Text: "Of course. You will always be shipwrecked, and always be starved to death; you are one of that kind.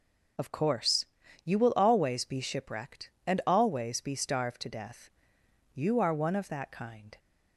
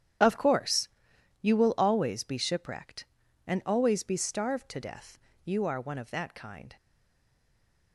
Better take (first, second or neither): first